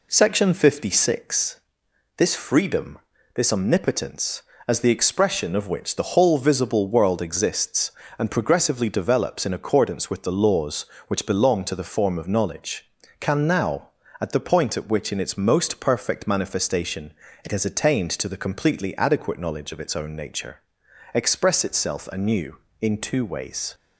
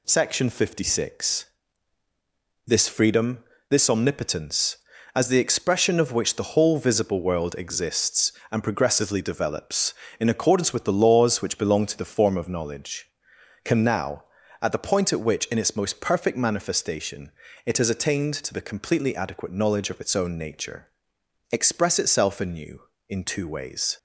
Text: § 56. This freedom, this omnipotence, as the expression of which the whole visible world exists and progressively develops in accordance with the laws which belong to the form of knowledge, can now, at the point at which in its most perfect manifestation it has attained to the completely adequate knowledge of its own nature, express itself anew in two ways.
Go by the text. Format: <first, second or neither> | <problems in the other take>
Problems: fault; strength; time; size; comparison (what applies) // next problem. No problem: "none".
neither | pauses between "manifestation" and "it"; slight; the same in both